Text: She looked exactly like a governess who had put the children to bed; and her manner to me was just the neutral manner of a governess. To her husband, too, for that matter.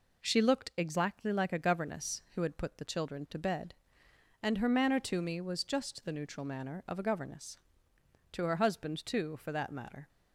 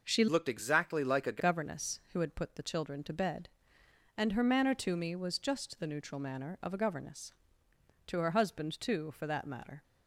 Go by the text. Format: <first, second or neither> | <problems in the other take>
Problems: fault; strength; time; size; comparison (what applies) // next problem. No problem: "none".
first | changes voice from "looked" to "a"; from 0.2 to 1.4 s; 1.2 s long